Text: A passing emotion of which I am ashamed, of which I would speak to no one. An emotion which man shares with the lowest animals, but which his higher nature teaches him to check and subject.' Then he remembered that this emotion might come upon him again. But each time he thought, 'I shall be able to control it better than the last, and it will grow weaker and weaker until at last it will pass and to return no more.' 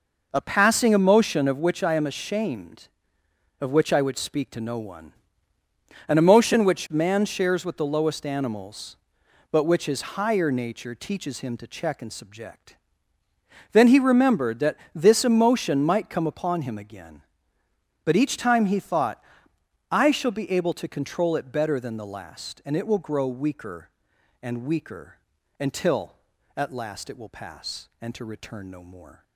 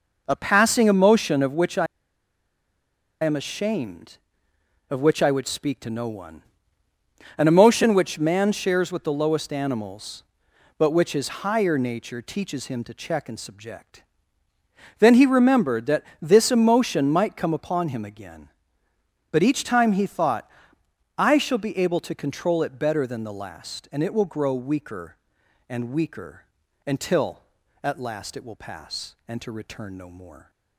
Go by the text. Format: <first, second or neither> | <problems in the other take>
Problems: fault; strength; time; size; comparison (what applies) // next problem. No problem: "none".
first | pauses between "I" and "am"; strong; at 1.8 s; 1.3 s long // pauses between "that" and "this"; slight; at 16.0 s; 0.18 s long; slight in the first // pauses between "weaker" and "until"; at 26.4 s; 0.42 s long; also in the first